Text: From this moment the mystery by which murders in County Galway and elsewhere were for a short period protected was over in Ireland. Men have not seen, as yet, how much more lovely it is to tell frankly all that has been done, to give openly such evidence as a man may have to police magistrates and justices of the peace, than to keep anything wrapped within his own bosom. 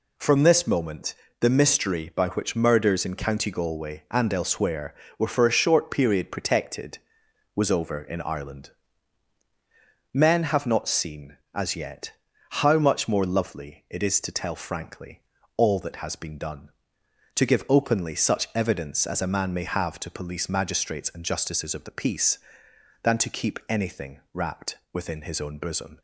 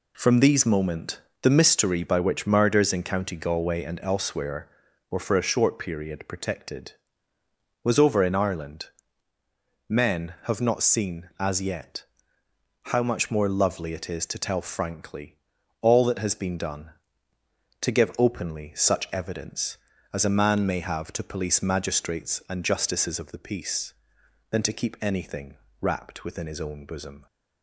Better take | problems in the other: first | says "these" for "this"; at 0.3 s // pauses between "moment" and "the"; slight; at 1.1 s; 0.22 s long; slight in the first // pauses between "frankly" and "all"; noticeable; at 15.3 s; 0.46 s long; slight in the first // pauses between "anything" and "wrapped"; slight; at 25.5 s; 0.24 s long

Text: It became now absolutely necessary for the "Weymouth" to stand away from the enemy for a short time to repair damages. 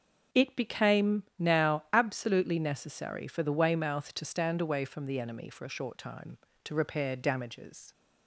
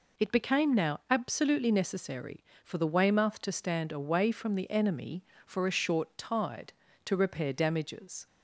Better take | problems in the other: first | says "tide" for "time"; at 6.1 s

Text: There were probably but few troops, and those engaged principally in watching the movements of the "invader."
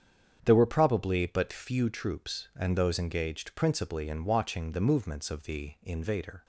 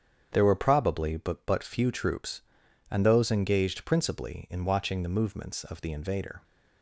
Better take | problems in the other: first | starts louder than the rest; strong; until 1.3 s; 8 dB; strong in the first // says "but" twice; at 1.4 s

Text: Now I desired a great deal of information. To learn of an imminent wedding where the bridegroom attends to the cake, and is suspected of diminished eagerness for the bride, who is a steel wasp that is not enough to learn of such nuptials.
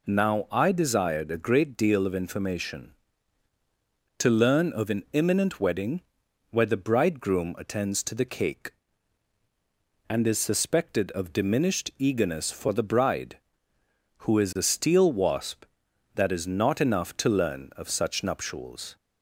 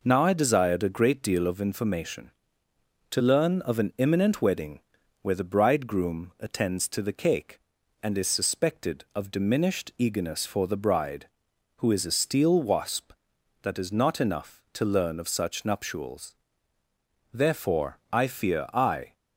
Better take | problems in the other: first | pauses between "wedding" and "where"; at 4.8 s; 0.40 s long; noticeable in the first // goes on to say "Therefore I fear I"; strong; from 17.3 s on; 1.8 s long

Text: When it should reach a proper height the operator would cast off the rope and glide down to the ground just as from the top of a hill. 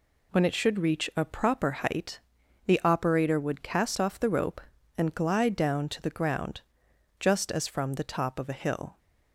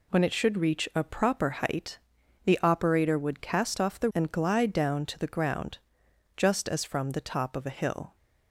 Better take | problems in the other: first | pauses between "height" and "the"; noticeable; at 1.9 s; 0.48 s long; noticeable in the first // skips "rope"; at 4.1 s // pauses between "ground" and "just"; noticeable; at 5.7 s; 0.58 s long; noticeable in the first

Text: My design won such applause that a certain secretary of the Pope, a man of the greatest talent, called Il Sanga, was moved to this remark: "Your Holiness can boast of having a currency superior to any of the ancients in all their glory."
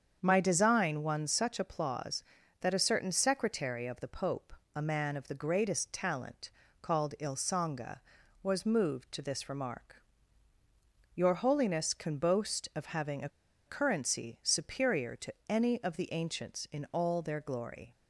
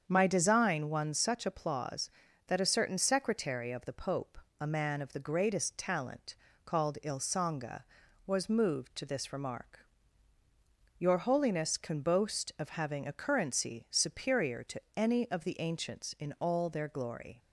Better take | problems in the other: second | starts louder than the rest; strong; until 1.2 s; 7.5 dB; strong in the second // pauses between "a" and "currency"; at 13.2 s; 0.38 s long // pauses between "to" and "any"; slight; at 15.3 s; 0.16 s long; slight in the second

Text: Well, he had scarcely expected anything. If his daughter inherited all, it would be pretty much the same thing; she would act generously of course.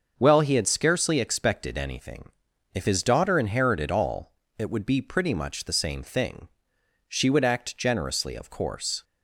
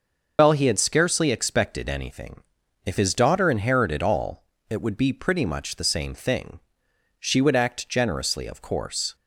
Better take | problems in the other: first | loses the start of "Well"; at 0.3 s; 100 ms // starts louder than the rest; noticeable; until 1.3 s; 6 dB; also in the first

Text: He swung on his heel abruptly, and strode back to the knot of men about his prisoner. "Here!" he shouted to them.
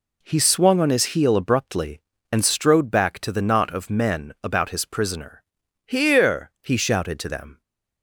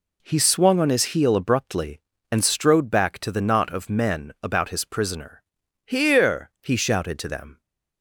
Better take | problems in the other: neither | none

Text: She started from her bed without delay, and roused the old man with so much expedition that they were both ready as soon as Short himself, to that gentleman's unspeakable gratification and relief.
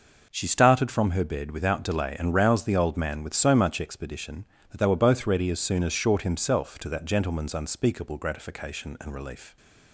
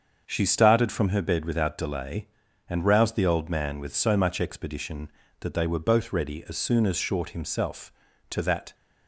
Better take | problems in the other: first | starts louder than the rest; until 1.2 s; 7 dB // stops before "gentleman's unspeakable gratification and relief"; at 8.7 s

